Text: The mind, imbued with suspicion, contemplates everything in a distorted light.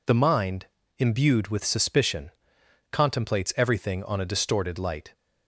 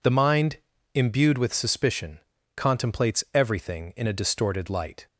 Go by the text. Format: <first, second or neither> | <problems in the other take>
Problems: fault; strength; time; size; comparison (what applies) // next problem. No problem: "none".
second | says "on" for "in"; at 4.0 s